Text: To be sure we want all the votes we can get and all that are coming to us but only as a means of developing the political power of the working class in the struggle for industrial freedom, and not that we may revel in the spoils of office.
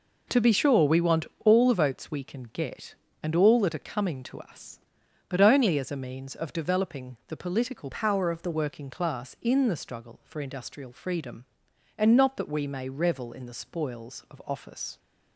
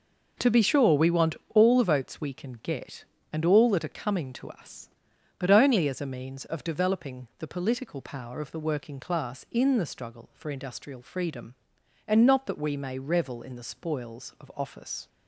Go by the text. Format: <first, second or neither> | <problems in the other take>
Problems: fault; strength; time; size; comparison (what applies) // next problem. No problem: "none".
second | pauses between "want" and "all"; slight; at 1.2 s; 0.20 s long; slight in the second // changes voice from "power" to "the"; from 7.9 to 8.4 s; 0.5 s long